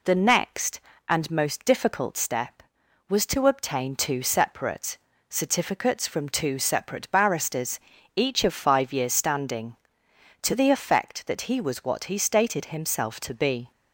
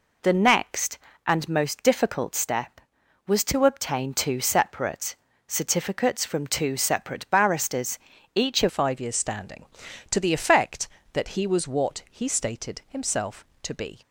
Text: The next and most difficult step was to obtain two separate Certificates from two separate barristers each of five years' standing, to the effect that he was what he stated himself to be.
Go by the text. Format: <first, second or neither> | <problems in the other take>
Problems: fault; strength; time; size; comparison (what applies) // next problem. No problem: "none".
first | pauses between "separate" and "Certificates"; slight; at 5.1 s; 0.32 s long; slight in the first // pauses between "barristers" and "each"; at 7.9 s; 0.38 s long; also in the first // changes voice at "five"; from 8.6 s on; 5.4 s long